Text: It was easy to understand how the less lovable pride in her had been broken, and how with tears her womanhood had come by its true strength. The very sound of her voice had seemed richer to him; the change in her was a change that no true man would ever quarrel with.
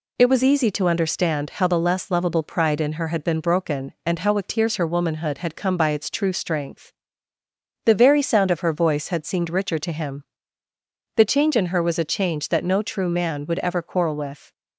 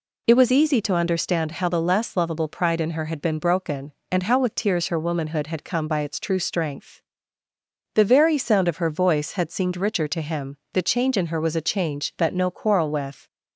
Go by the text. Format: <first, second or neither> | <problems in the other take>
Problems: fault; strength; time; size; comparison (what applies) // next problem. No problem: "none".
first | skips "true man would ever"; at 12.5 s